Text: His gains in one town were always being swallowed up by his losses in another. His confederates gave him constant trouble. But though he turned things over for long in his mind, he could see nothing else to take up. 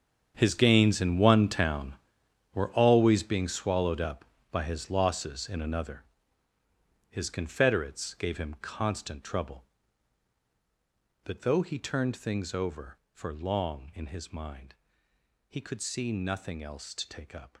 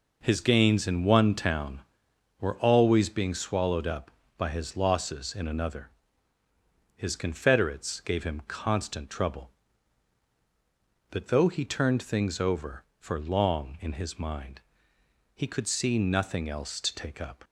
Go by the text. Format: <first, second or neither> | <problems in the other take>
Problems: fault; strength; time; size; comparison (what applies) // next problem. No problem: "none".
second | gets quieter; strong; throughout; 15 dB